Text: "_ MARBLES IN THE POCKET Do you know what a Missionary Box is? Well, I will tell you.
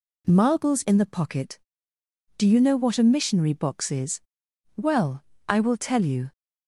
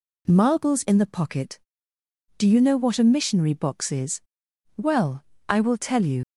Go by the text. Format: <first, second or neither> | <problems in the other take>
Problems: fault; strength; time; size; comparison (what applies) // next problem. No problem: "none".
first | leaves "you" unfinished; at 6.2 s; 90 ms